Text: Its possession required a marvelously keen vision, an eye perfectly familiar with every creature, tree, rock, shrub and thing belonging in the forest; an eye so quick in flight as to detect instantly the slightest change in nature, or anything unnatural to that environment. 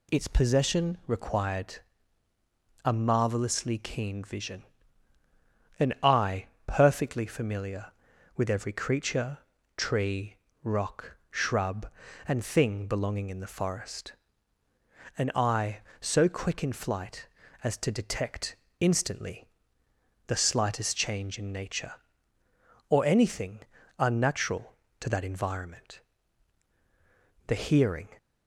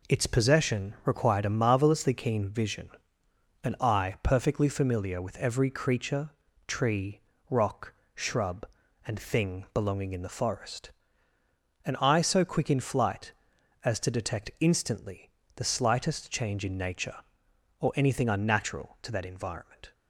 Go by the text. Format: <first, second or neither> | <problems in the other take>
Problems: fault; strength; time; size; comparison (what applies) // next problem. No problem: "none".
second | pauses between "required" and "a"; at 1.7 s; 1.0 s long // pauses between "eye" and "perfectly"; slight; at 6.4 s; 0.20 s long // pauses between "detect" and "instantly"; slight; at 18.5 s; 0.24 s long // pauses between "instantly" and "the"; noticeable; at 19.4 s; 0.80 s long; slight in the second // pauses between "anything" and "unnatural"; at 23.5 s; 0.40 s long // goes on to say "The hearing"; noticeable; from 27.4 s on; 0.62 s long